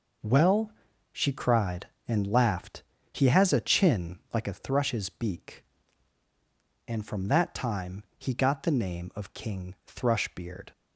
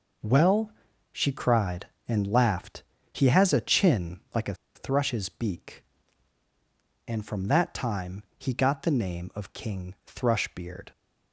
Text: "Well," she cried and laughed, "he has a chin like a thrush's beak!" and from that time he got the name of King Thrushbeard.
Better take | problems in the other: first | pauses between "chin" and "like"; slight; at 4.1 s; 0.16 s long; slight in the first // pauses between "a" and "thrush's"; slight; at 4.5 s; 0.20 s long // pauses between "time" and "he"; slight; at 8.2 s; 0.16 s long; slight in the first

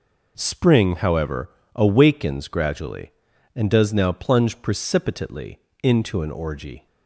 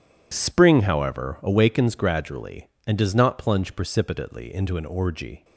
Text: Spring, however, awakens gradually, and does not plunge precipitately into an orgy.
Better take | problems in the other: second | says "now" for "not"; at 3.9 s // pauses between "precipitately" and "into"; slight; at 5.5 s; 0.24 s long

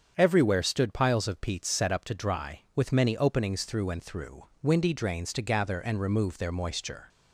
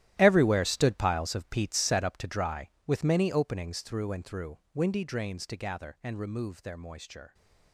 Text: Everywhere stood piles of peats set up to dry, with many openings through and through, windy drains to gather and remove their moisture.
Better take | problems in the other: first | gets quieter; strong; throughout; 14 dB // starts louder than the rest; strong; until 1.2 s; 13 dB; strong in the first

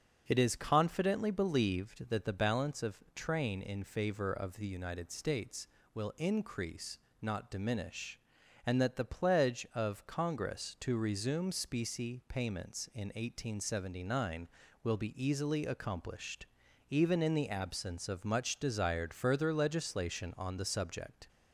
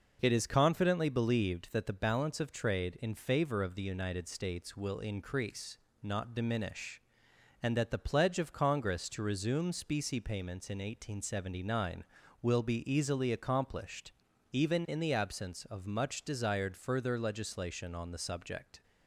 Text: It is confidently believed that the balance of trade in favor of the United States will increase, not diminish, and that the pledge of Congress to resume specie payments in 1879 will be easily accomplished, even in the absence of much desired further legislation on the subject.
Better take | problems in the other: second | starts louder than the rest; until 1.2 s; 7 dB // says "train" for "trade"; at 3.1 s

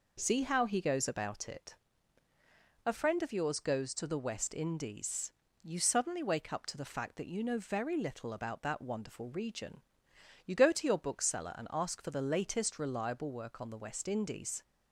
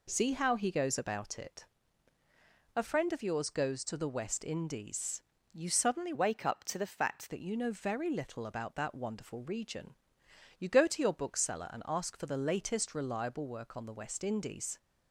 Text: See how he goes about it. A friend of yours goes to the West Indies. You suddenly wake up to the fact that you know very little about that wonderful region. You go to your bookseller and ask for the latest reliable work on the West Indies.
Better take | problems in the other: first | changes voice from "wake" to "fact"; from 6.1 to 7.3 s; 1.2 s long

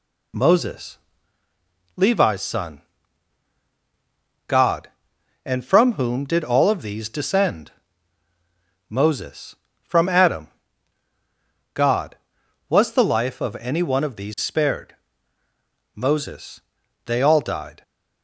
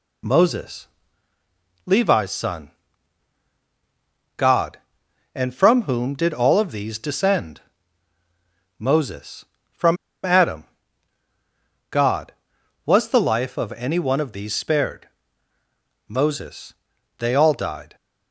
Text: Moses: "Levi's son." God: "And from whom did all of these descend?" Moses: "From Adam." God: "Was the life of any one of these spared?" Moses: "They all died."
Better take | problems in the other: first | pauses between "From" and "Adam"; slight; at 9.9 s; 0.28 s long

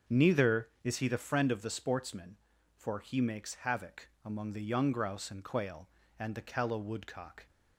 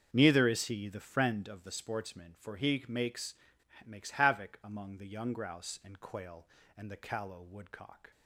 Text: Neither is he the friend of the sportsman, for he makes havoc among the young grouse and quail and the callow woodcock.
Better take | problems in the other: first | starts louder than the rest; until 1.1 s; 6.5 dB; also in the first // says "makes" twice; at 3.8 s

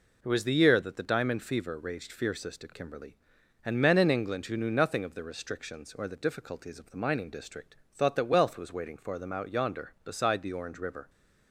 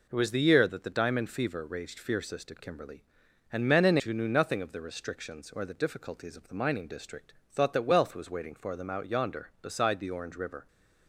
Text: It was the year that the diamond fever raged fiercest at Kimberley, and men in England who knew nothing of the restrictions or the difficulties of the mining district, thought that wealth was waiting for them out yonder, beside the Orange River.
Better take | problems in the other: first | skips "England"; at 4.0 s

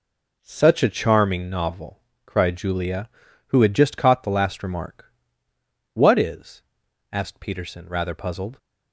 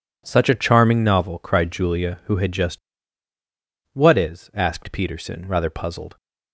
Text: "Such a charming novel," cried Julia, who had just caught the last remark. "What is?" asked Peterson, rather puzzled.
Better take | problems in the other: first | skips "caught the last remark"; at 3.3 s

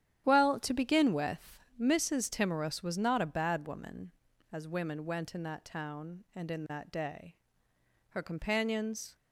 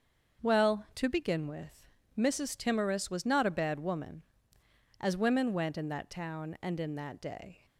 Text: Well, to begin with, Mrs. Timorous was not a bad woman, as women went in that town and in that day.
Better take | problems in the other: second | starts louder than the rest; strong; until 1.2 s; 10.5 dB; also in the second // goes on to say "Her companions"; noticeable; from 8.0 s on; 1.0 s long

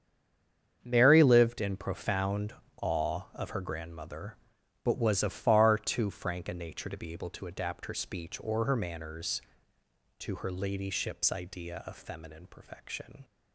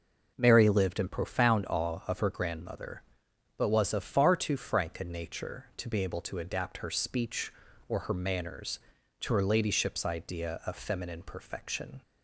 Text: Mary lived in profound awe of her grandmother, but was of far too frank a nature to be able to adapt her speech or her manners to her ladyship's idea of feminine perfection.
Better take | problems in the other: second | stays silent before the first word; slight; until 0.8 s; 0.8 s long // starts louder than the rest; strong; until 1.8 s; 7.5 dB // pauses between "profound" and "awe"; slight; at 2.5 s; 0.26 s long

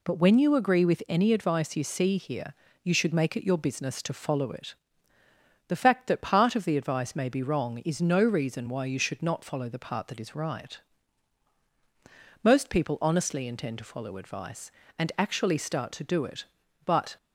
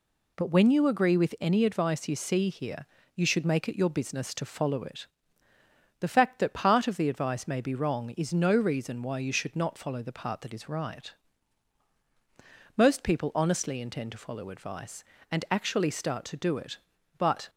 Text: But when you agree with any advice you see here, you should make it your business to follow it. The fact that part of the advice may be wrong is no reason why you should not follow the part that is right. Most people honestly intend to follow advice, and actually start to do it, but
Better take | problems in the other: neither | none

